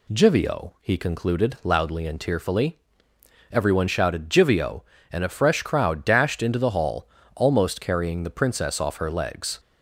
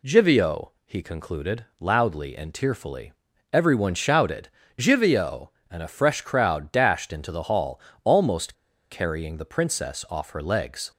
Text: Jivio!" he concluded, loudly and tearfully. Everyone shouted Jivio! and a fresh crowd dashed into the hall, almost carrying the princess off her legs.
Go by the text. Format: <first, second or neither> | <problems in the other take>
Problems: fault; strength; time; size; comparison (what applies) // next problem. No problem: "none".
first | pauses between "shouted" and "Jivio"; slight; at 4.4 s; 0.28 s long // pauses between "almost" and "carrying"; at 8.5 s; 0.38 s long